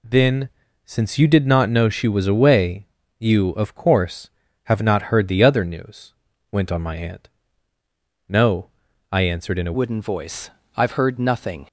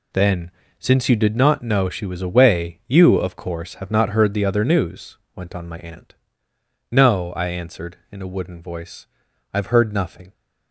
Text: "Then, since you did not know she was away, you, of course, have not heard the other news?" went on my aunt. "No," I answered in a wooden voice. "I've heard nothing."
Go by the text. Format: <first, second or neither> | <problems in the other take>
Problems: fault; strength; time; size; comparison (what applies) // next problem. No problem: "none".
second | changes voice at "wooden"; from 9.7 s on; 1.9 s long